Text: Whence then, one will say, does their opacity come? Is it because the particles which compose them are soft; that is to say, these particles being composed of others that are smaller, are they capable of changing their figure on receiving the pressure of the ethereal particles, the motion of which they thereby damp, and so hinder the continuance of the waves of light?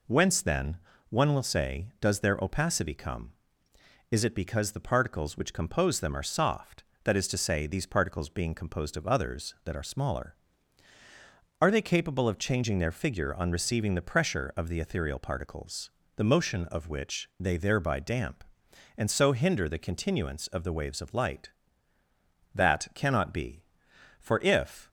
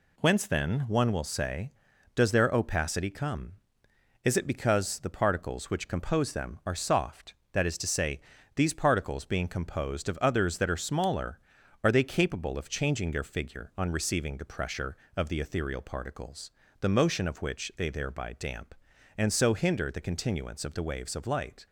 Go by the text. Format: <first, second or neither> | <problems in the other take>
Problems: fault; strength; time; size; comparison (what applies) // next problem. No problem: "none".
second | goes on to say "That cannot be for if"; strong; from 22.5 s on; 2.3 s long